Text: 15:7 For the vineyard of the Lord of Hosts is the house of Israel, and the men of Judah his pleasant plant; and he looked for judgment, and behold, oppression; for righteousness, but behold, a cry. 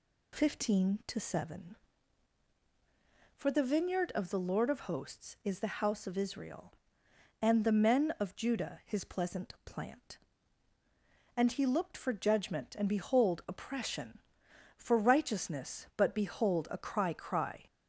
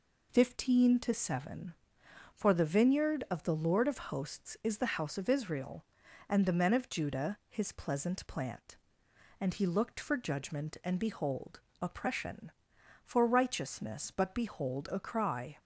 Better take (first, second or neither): second